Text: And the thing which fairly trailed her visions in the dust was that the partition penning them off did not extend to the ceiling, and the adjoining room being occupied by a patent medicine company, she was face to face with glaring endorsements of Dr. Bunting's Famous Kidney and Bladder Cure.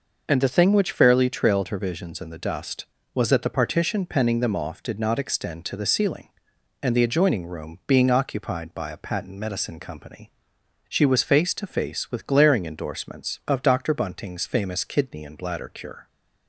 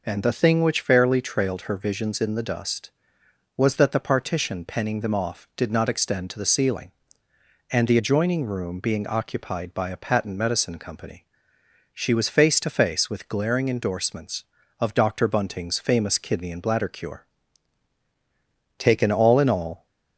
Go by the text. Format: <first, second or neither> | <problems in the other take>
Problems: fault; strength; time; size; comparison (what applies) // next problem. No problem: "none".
first | goes on to say "Taken all in all"; noticeable; from 18.7 s on; 1.0 s long